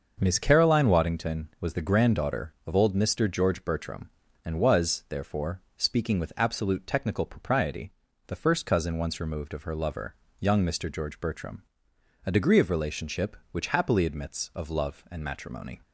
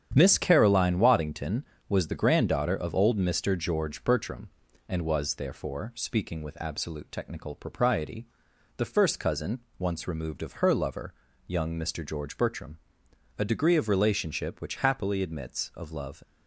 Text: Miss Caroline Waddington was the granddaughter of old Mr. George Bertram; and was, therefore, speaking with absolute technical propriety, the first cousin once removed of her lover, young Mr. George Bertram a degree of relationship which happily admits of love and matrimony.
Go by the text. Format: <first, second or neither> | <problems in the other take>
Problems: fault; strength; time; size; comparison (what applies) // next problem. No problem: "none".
first | starts louder than the rest; strong; until 1.1 s; 9 dB; also in the first // pauses between "cousin" and "once"; slight; at 9.6 s; 0.18 s long // pauses between "Bertram" and "a"; noticeable; at 12.7 s; 0.62 s long; noticeable in the first // stops before "and matrimony"; at 16.2 s